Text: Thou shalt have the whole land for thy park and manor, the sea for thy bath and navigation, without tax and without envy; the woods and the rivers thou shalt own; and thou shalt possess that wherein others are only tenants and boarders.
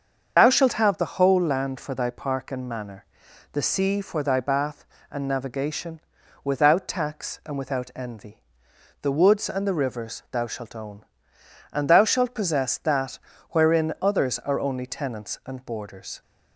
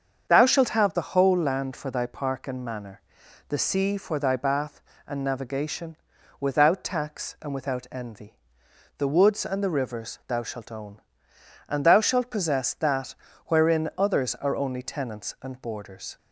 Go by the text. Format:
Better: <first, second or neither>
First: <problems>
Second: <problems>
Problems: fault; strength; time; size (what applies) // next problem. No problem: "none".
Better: second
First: loses the start of "Thou"; at 0.3 s; 35 ms // starts louder than the rest; until 1.3 s; 7 dB // pauses between "that" and "wherein"; slight; at 13.1 s; 0.32 s long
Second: starts louder than the rest; until 1.3 s; 7 dB // pauses between "that" and "wherein"; slight; at 13.1 s; 0.32 s long